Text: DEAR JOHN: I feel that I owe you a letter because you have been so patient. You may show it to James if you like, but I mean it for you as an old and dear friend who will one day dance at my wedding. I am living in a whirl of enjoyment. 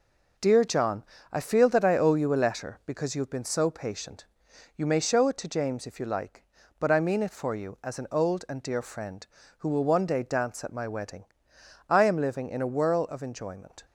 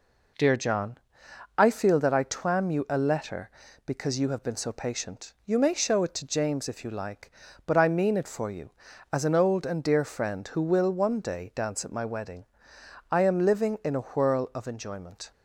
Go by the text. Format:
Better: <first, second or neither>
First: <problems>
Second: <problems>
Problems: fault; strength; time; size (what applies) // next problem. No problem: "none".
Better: first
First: none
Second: says "twam" for "owe"; at 2.2 s